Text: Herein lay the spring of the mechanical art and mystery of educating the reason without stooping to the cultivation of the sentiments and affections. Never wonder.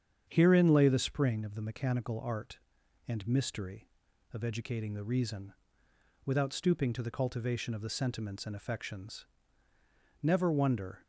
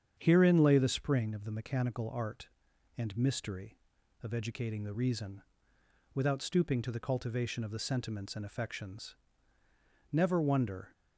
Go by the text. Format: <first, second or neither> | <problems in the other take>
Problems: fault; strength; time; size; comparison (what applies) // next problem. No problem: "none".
neither | starts louder than the rest; strong; the same in both // pauses between "reason" and "without"; noticeable; the same in both